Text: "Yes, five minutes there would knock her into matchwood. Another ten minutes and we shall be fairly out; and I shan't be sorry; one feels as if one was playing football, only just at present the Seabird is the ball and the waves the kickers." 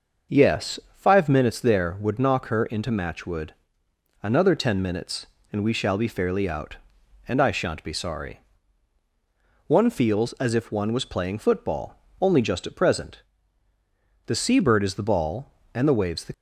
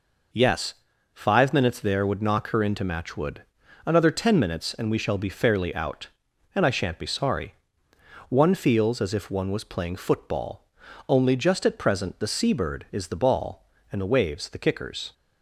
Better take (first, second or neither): second